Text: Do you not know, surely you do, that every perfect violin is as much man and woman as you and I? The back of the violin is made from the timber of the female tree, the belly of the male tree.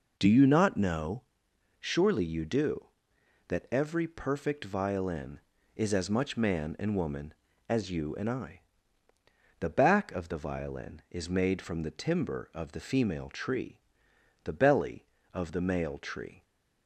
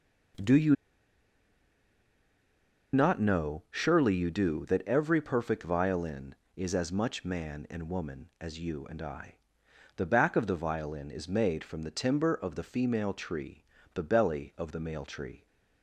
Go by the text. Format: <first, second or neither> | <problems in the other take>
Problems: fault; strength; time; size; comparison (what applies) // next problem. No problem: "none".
first | pauses between "you" and "not"; strong; at 0.7 s; 2.1 s long